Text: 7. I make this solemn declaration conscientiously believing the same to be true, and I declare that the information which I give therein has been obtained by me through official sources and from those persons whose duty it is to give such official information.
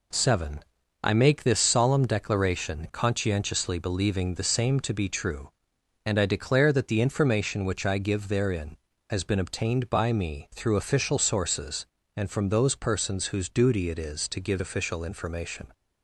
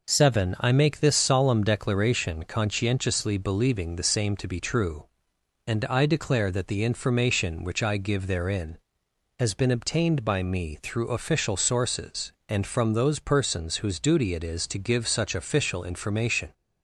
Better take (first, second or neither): second